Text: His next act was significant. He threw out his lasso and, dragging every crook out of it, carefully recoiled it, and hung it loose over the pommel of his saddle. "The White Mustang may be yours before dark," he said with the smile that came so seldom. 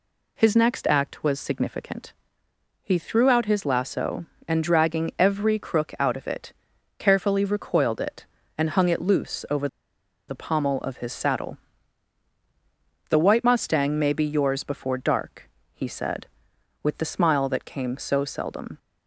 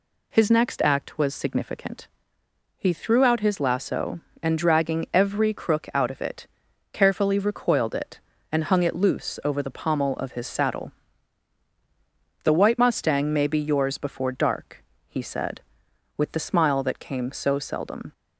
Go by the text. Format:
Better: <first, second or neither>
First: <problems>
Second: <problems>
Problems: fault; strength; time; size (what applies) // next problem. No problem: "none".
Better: second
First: pauses between "over" and "the"; noticeable; at 9.6 s; 0.61 s long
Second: none